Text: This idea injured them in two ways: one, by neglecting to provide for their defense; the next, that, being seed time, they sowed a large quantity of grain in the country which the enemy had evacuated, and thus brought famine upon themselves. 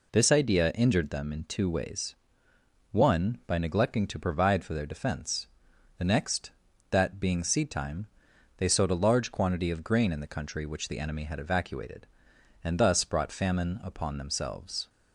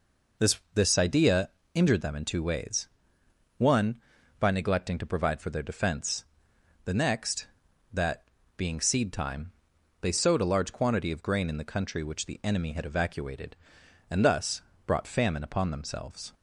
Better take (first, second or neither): first